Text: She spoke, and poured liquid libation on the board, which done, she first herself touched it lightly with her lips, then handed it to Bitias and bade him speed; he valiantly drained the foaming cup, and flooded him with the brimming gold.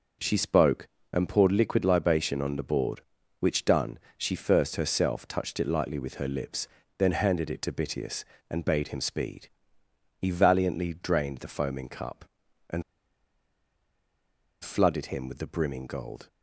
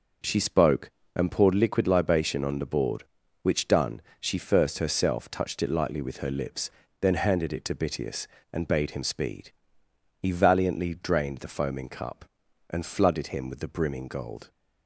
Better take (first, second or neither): second